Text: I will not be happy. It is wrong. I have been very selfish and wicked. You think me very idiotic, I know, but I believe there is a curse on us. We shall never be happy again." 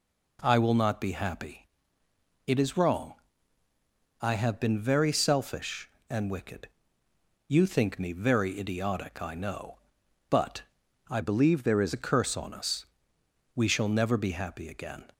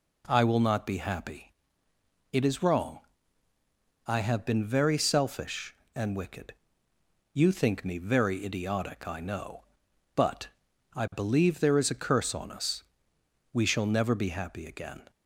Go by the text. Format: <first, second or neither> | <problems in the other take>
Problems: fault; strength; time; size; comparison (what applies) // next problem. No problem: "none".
second | pauses between "but" and "I"; noticeable; at 10.6 s; 0.48 s long; noticeable in the second // changes voice from "believe" to "is"; from 11.2 to 11.9 s; 0.7 s long